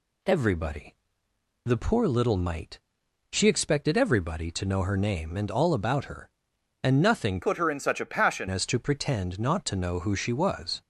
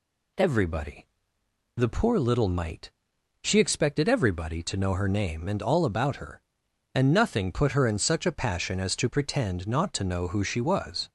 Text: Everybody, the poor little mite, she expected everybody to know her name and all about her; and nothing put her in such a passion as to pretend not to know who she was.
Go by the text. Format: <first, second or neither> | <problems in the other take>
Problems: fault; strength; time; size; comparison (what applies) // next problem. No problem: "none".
second | changes voice from "put" to "passion"; from 7.4 to 8.4 s; 1.0 s long